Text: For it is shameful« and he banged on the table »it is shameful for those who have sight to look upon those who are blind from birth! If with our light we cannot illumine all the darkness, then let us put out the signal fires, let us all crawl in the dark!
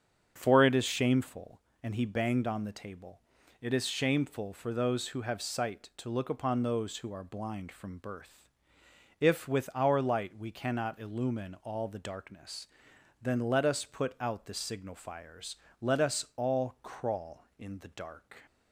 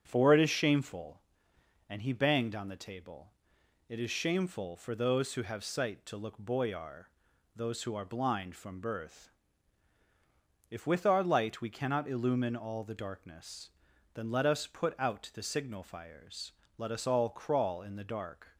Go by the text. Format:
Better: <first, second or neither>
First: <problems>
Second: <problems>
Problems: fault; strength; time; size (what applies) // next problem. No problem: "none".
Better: first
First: starts louder than the rest; strong; until 1.3 s; 8 dB // pauses between "table" and "it"; at 3.2 s; 0.38 s long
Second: starts louder than the rest; until 1.0 s; 7 dB // pauses between "table" and "it"; noticeable; at 3.3 s; 0.56 s long // says "boyar" for "upon"; at 6.3 s